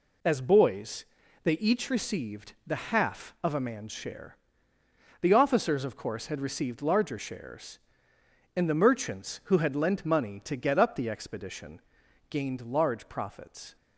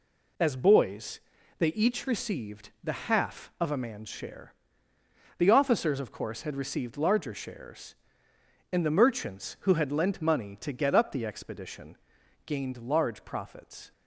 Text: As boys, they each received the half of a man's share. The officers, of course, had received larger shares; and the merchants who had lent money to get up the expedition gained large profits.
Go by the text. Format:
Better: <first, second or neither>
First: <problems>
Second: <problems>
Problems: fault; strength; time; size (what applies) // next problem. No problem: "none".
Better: neither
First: pauses between "expedition" and "gained"; noticeable; at 11.7 s; 0.52 s long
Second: pauses between "expedition" and "gained"; noticeable; at 11.9 s; 0.52 s long